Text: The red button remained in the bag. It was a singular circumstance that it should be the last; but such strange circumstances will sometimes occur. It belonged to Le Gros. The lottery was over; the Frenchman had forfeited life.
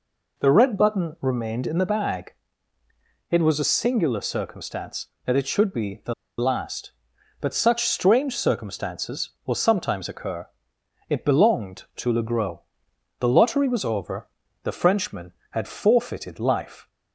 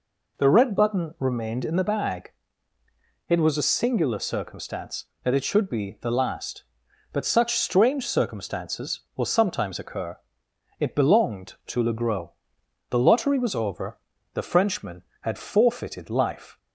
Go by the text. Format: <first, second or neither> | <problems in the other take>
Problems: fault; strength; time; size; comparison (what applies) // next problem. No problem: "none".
second | pauses between "the" and "last"; slight; at 6.1 s; 0.25 s long